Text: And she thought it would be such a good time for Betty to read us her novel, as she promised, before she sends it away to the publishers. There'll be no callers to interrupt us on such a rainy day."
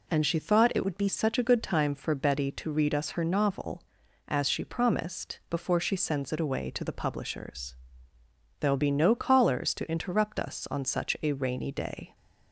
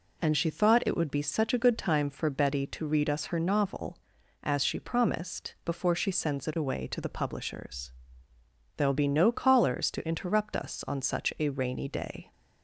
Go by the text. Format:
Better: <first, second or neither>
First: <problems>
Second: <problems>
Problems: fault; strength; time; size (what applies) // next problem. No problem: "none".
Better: second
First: changes voice from "would" to "be"; from 0.8 to 1.0 s; 0.2 s long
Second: none